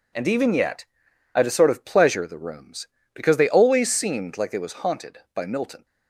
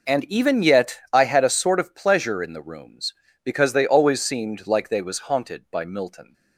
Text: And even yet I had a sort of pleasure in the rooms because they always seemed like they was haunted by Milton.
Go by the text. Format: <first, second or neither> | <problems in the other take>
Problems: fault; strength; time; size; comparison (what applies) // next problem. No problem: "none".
second | pauses between "yet" and "I"; noticeable; at 0.8 s; 0.50 s long // skips "in"; at 2.2 s